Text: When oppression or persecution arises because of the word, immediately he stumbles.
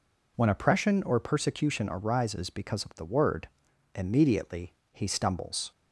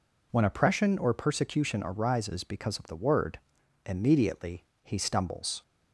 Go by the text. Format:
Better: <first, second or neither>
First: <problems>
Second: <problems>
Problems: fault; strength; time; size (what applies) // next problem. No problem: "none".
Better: neither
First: pauses between "immediately" and "he"; slight; at 4.7 s; 0.18 s long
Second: pauses between "immediately" and "he"; slight; at 4.6 s; 0.18 s long